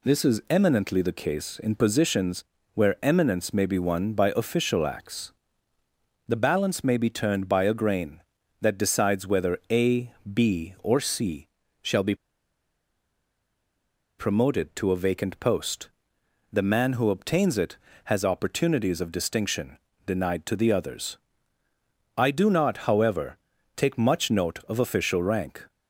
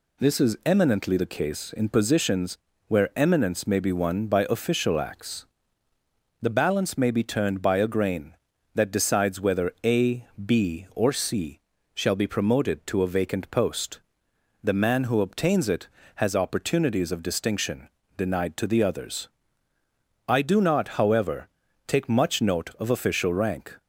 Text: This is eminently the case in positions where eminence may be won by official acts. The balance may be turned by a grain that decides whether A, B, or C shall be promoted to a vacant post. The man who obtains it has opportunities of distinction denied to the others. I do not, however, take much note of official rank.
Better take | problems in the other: second | pauses between "positions" and "where"; slight; at 2.4 s; 0.30 s long; slight in the second // pauses between "C" and "shall"; slight; at 11.4 s; 0.34 s long; slight in the second // pauses between "be" and "promoted"; strong; at 12.1 s; 2.0 s long // pauses between "distinction" and "denied"; slight; at 19.7 s; 0.28 s long; slight in the second

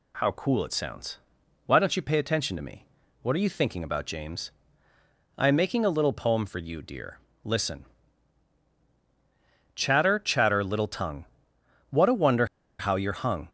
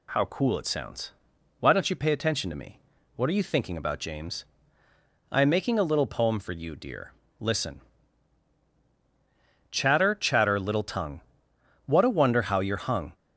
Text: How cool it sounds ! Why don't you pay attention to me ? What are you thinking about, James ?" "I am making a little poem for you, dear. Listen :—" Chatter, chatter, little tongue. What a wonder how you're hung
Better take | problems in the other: second | pauses between "wonder" and "how"; slight; at 12.4 s; 0.33 s long

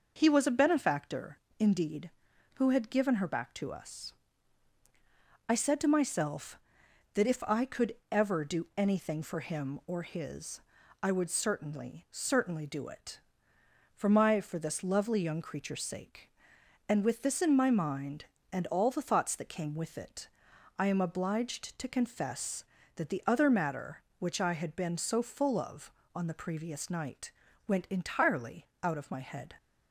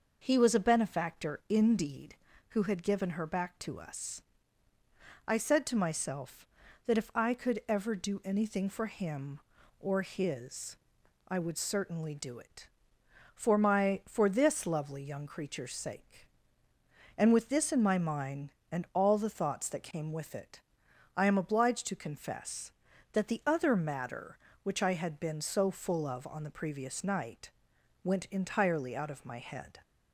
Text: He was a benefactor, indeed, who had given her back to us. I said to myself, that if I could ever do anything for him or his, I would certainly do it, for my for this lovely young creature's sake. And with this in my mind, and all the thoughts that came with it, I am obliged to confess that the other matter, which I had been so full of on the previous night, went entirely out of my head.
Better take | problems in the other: second | says "certainly" twice; at 12.1 s

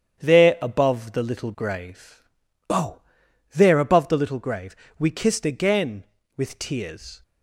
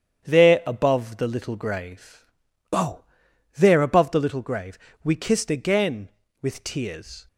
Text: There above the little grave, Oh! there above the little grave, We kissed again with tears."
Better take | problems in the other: neither | starts louder than the rest; strong; the same in both

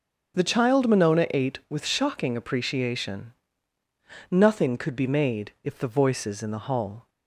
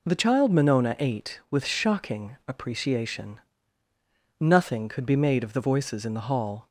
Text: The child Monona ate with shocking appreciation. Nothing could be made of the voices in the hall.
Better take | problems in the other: second | starts louder than the rest; until 1.3 s; 6.5 dB // says "if" for "of"; at 5.6 s

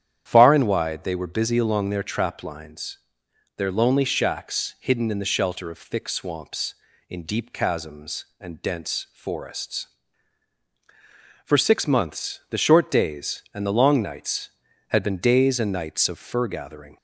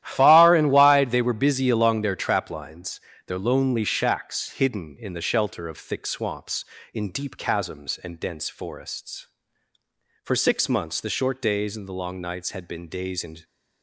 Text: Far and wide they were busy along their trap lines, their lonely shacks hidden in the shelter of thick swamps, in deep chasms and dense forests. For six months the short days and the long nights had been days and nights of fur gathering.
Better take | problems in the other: first | starts louder than the rest; strong; until 1.0 s; 12.5 dB; strong in the first // stops before "nights of fur gathering"; at 13.4 s

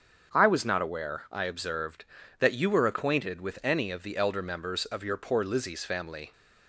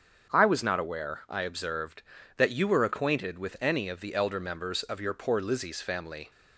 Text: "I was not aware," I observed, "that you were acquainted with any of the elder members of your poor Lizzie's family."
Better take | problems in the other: neither | starts louder than the rest; strong; the same in both

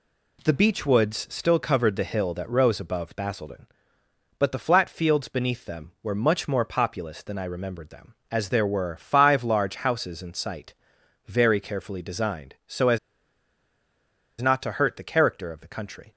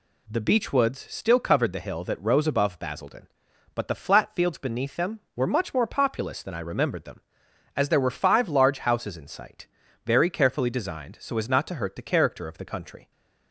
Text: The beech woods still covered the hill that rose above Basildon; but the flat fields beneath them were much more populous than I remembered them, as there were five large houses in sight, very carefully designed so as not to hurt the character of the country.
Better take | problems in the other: second | pauses between "as" and "not"; strong; at 12.9 s; 1.4 s long

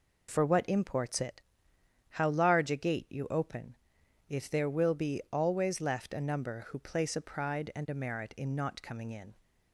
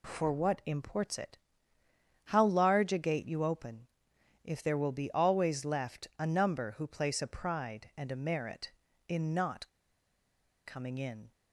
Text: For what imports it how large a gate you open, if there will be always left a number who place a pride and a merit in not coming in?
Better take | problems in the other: first | pauses between "it" and "how"; noticeable; at 1.3 s; 0.86 s long; noticeable in the first // pauses between "not" and "coming"; at 9.6 s; 0.98 s long

